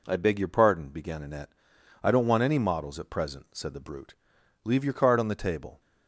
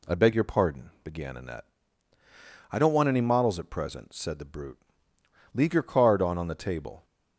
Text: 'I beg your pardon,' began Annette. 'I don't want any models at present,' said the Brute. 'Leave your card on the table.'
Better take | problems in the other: first | says "on" twice; at 6.3 s

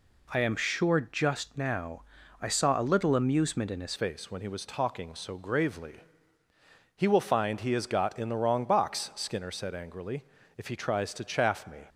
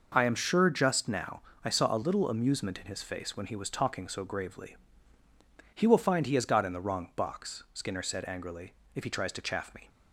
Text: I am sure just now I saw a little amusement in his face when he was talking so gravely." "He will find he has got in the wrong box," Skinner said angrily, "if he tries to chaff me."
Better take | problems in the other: second | pauses between "now" and "I"; at 2.0 s; 0.38 s long; slight in the second // changes voice at "face"; from 3.9 s on; 7.9 s long

